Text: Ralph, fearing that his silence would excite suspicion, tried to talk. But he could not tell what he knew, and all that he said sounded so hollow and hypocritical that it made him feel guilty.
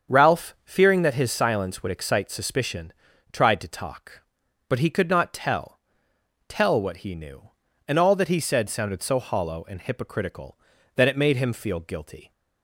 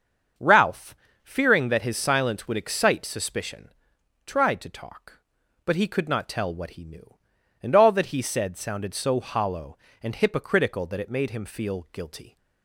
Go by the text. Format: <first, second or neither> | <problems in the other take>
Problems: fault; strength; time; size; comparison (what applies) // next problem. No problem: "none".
second | starts louder than the rest; until 1.2 s; 7 dB; also in the second // says "tell" twice; at 6.4 s